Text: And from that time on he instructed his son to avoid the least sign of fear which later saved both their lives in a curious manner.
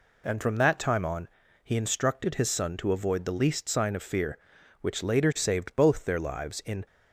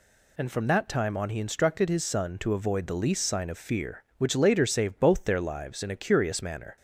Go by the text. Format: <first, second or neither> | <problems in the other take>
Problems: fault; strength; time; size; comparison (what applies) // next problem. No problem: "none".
second | pauses between "on" and "he"; slight; at 1.2 s; 0.34 s long // stops before "a curious manner"; at 6.8 s